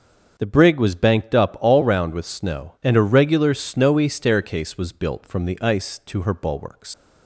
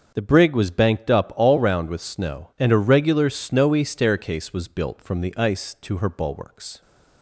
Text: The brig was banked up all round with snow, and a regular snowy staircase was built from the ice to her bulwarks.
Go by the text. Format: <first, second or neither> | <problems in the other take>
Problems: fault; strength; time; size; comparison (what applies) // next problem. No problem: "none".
second | starts louder than the rest; until 1.3 s; 6.5 dB; also in the second // leaves "bulwarks" unfinished; at 6.9 s; 110 ms